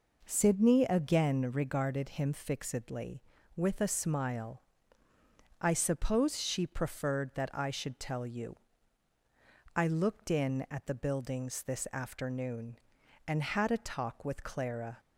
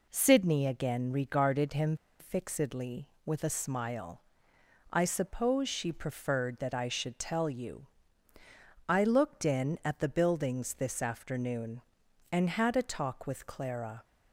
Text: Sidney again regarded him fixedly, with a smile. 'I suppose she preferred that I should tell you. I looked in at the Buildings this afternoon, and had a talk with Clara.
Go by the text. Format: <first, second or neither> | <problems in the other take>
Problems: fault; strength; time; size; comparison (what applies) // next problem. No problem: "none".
first | pauses between "him" and "fixedly"; slight; at 1.9 s; 0.23 s long